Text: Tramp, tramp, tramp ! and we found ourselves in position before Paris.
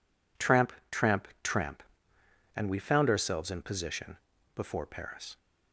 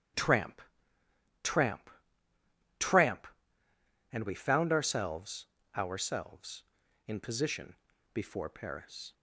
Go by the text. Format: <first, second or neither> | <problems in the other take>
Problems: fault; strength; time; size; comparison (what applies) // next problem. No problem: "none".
first | starts louder than the rest; strong; until 2.8 s; 9.5 dB // says "ourselves" twice; at 5.7 s // pauses between "position" and "before"; at 7.7 s; 0.38 s long; slight in the first